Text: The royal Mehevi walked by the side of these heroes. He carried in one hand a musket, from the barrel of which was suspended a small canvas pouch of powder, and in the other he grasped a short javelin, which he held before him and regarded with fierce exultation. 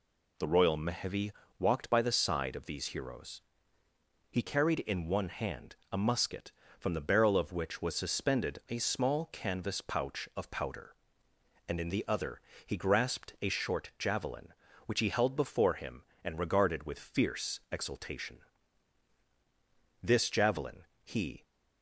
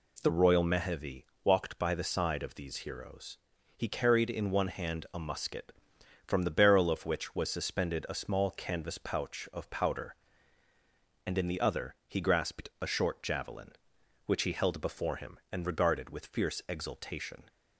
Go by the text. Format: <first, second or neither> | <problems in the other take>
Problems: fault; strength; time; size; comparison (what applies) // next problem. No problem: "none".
second | pauses between "Mehevi" and "walked"; slight; at 1.3 s; 0.26 s long; slight in the second // pauses between "hand" and "a"; slight; at 5.7 s; 0.16 s long // pauses between "other" and "he"; slight; at 12.4 s; 0.24 s long // goes on to say "This javelin he"; from 20.0 s on; 1.4 s long